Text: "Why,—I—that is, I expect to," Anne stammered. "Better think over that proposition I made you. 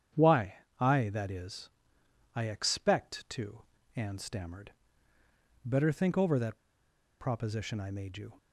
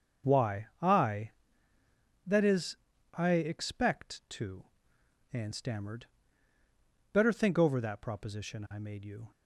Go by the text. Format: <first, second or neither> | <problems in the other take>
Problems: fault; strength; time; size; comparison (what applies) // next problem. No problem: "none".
second | starts louder than the rest; strong; until 1.4 s; 8.5 dB; also in the second // pauses between "that" and "proposition"; noticeable; at 6.5 s; 0.61 s long